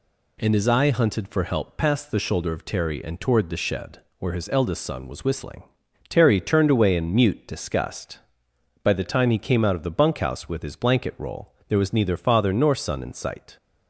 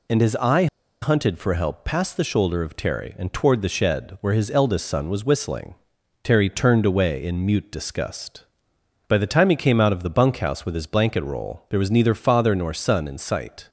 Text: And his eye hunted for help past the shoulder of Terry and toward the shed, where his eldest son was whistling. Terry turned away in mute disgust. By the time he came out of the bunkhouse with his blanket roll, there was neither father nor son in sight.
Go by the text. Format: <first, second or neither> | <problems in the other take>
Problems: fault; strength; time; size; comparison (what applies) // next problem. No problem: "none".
first | pauses between "eye" and "hunted"; slight; at 0.6 s; 0.36 s long